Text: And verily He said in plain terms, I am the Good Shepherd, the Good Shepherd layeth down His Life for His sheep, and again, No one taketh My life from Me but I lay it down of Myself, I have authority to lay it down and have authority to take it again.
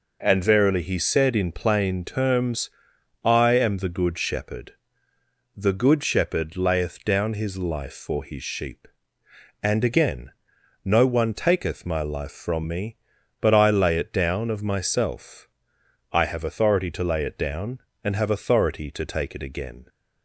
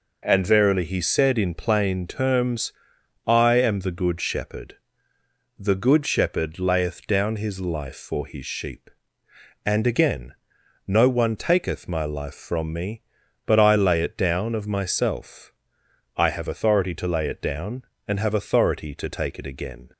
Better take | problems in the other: neither | none

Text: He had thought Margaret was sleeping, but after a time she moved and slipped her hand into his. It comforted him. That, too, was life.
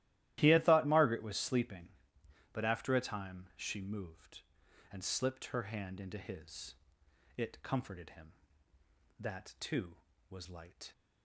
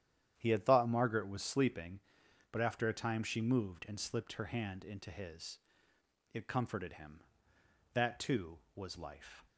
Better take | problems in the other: second | starts louder than the rest; strong; until 1.4 s; 14.5 dB; strong in the second // says "light" for "life"; at 10.4 s

